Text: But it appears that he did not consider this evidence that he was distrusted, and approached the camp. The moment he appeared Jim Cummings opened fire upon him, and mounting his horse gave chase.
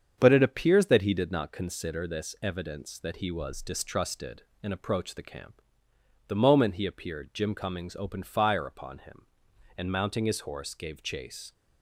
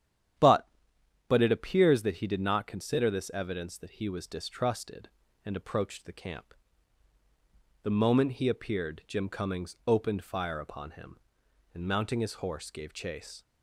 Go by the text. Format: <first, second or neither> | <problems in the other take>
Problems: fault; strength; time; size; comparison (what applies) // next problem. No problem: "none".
first | starts louder than the rest; strong; until 2.0 s; 10 dB; strong in the first // says "But" twice; at 1.2 s